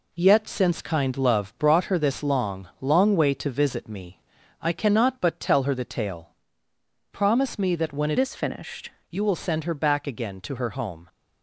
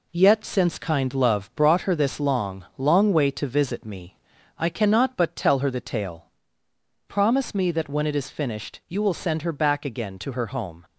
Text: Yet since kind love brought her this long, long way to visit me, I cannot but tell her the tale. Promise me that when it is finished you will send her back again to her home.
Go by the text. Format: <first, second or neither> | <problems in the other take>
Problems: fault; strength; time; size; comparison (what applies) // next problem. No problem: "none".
second | changes voice from "is" to "finished"; from 8.1 to 8.8 s; 0.7 s long